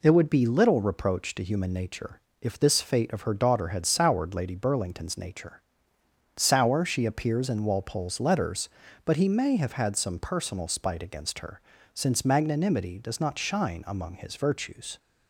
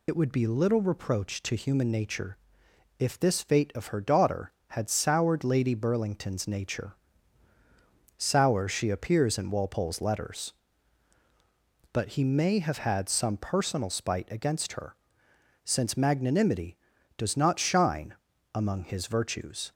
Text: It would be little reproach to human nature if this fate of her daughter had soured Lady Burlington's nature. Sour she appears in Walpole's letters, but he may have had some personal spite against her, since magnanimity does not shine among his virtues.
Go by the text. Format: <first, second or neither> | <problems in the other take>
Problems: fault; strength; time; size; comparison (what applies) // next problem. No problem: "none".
first | loses the start of "It"; at 0.0 s; 75 ms // pauses between "nature" and "if"; noticeable; at 2.3 s; 0.60 s long; slight in the first // pauses between "shine" and "among"; at 18.1 s; 0.40 s long